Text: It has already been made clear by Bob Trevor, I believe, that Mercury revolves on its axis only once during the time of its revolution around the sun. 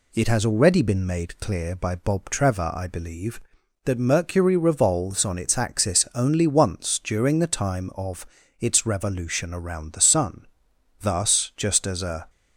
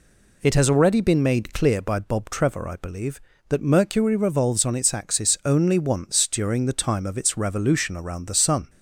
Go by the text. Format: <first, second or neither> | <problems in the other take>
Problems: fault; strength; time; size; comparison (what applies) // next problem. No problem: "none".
second | pauses between "of" and "its"; slight; at 8.2 s; 0.34 s long // goes on to say "Thus just as a"; noticeable; from 11.0 s on; 1.2 s long